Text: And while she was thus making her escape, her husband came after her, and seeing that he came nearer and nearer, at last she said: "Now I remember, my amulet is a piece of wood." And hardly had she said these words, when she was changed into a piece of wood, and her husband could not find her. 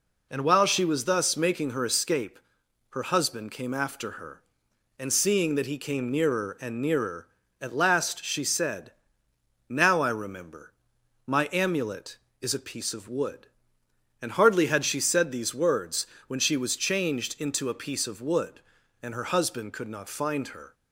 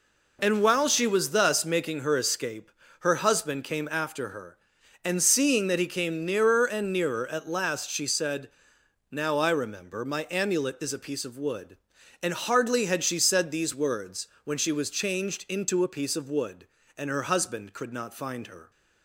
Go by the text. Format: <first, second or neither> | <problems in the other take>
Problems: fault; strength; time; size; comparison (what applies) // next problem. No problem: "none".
neither | none